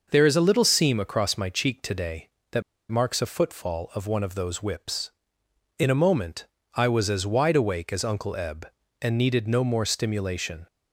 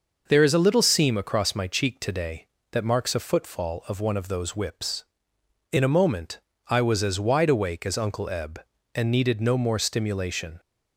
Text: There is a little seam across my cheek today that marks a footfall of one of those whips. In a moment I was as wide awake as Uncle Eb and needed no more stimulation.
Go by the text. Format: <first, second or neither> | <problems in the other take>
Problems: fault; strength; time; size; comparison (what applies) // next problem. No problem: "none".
second | pauses between "that" and "marks"; slight; at 2.6 s; 0.27 s long // pauses between "moment" and "I"; slight; at 6.4 s; 0.28 s long; slight in the second